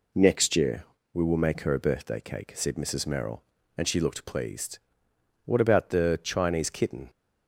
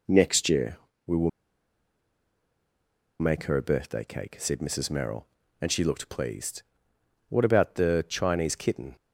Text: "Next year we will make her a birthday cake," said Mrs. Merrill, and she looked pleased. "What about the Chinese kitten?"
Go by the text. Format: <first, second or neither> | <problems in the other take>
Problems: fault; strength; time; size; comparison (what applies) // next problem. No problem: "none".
first | pauses between "year" and "we"; slight; at 0.7 s; 0.30 s long; slight in the first // pauses between "will" and "make"; strong; at 1.2 s; 1.9 s long